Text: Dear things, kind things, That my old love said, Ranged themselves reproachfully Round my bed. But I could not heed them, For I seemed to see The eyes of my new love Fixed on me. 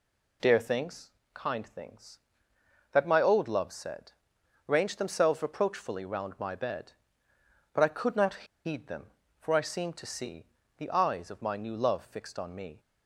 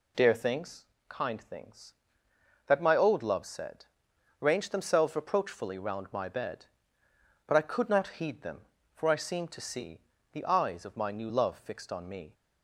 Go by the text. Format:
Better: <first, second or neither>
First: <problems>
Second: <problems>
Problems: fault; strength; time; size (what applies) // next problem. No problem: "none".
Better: second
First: pauses between "not" and "heed"; slight; at 8.4 s; 0.21 s long // pauses between "see" and "The"; slight; at 10.4 s; 0.34 s long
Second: pauses between "see" and "The"; slight; at 9.9 s; 0.34 s long